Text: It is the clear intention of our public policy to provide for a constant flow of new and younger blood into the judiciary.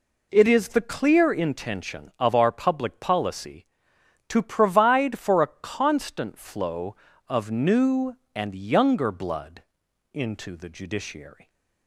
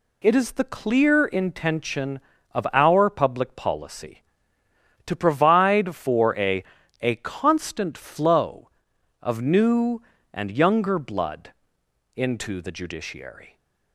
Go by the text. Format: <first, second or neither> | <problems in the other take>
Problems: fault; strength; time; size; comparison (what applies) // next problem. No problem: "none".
first | says "a" twice; at 7.0 s // pauses between "blood" and "into"; noticeable; at 11.5 s; 0.64 s long; noticeable in the first